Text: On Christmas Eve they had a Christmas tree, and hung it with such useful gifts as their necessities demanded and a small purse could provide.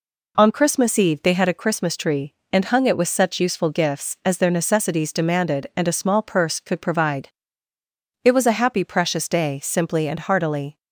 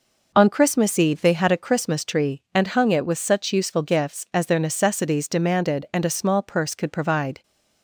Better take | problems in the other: second | goes on to say "It was a happy precious day simply and heartily"; strong; from 8.2 s on; 2.5 s long

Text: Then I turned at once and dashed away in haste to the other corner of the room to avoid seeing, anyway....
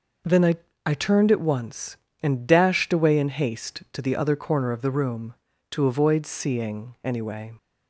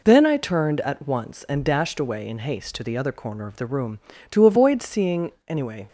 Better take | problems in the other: second | says "I" twice; at 0.8 s

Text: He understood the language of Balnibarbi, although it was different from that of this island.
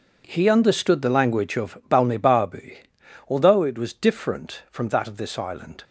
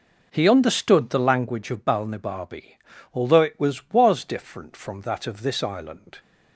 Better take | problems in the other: first | says "was" twice; at 3.8 s

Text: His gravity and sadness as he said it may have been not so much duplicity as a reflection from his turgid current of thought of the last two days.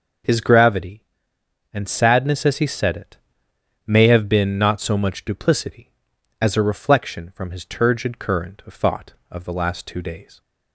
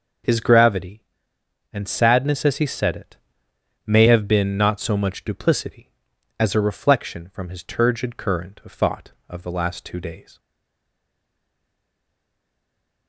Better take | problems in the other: first | pauses between "it" and "may"; noticeable; at 3.1 s; 0.68 s long; noticeable in the first // stays silent after the last word; strong; from 10.3 s on; 2.7 s long

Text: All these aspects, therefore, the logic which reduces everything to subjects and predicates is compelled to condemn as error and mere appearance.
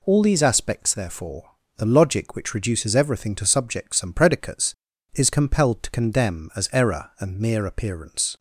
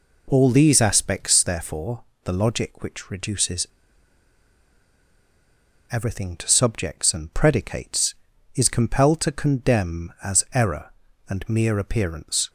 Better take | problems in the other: first | pauses between "reduces" and "everything"; strong; at 3.6 s; 2.2 s long

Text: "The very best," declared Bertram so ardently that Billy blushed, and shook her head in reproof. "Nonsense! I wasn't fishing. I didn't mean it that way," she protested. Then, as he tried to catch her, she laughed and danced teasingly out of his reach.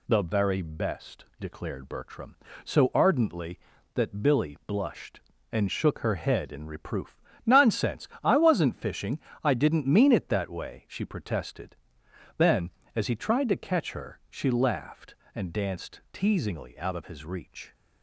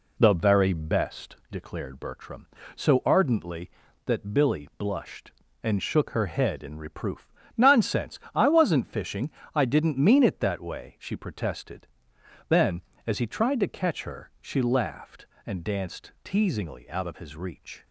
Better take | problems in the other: first | starts louder than the rest; slight; until 1.6 s; 2 dB

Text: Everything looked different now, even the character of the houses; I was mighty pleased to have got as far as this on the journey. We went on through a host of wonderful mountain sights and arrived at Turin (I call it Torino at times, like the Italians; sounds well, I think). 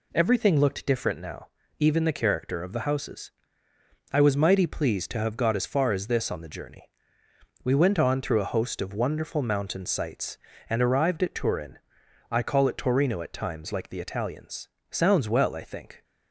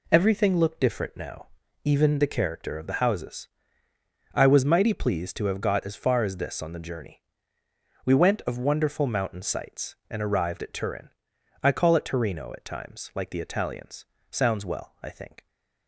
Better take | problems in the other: first | skips "on through a host"; at 8.4 s

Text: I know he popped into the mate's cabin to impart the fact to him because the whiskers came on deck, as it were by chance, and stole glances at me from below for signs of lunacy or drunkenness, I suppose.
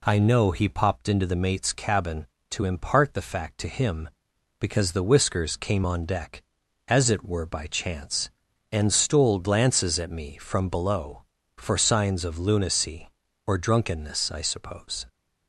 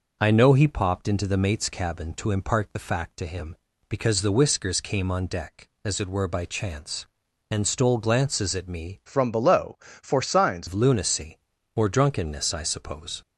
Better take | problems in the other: first | changes voice from "from" to "signs"; from 9.0 to 10.6 s; 1.6 s long

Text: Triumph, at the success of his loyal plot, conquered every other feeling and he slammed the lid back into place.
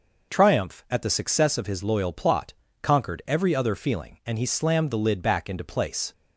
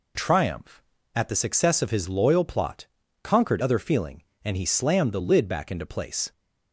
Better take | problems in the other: first | skips "every"; at 3.6 s

